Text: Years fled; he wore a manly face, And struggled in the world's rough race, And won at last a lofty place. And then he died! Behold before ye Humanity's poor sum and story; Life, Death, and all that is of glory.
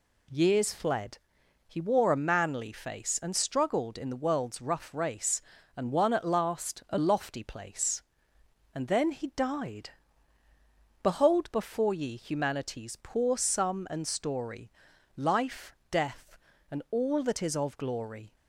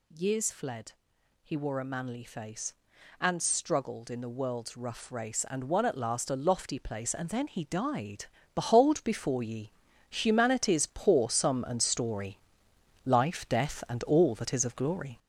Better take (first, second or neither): first